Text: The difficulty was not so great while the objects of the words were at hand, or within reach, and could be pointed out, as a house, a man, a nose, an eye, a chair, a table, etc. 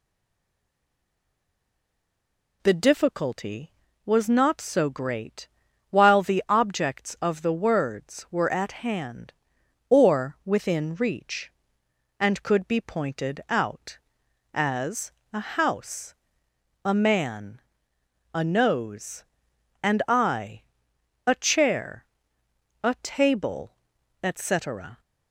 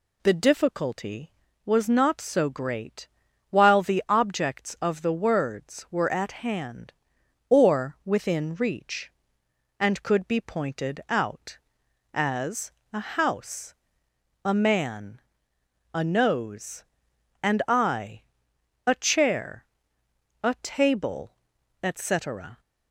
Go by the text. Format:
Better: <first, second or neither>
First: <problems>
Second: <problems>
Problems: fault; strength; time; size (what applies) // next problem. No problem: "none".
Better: second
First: stays silent before the first word; strong; until 2.6 s; 2.6 s long // pauses between "great" and "while"; at 5.4 s; 0.42 s long // pauses between "as" and "a"; slight; at 15.0 s; 0.22 s long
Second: pauses between "great" and "while"; at 3.0 s; 0.42 s long // pauses between "as" and "a"; slight; at 12.6 s; 0.22 s long